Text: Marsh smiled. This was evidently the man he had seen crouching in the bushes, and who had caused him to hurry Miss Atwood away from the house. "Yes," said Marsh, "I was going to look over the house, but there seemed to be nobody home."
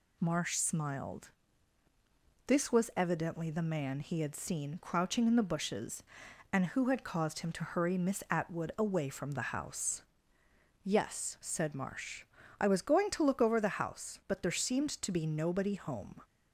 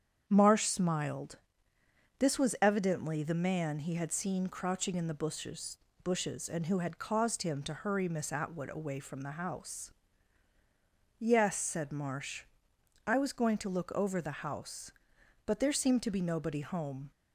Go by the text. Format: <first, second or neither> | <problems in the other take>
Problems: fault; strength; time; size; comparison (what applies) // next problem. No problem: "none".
first | starts louder than the rest; strong; until 1.2 s; 8 dB // says "bushes" twice; at 6.0 s